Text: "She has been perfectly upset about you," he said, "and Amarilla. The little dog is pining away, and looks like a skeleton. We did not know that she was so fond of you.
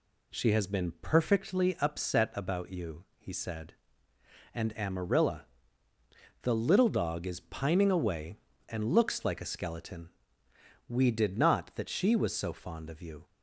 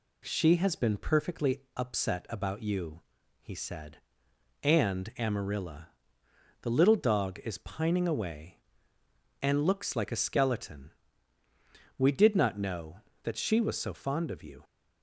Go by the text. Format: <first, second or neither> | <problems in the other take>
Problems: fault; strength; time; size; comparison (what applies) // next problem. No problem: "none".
second | skips "know"; at 11.7 s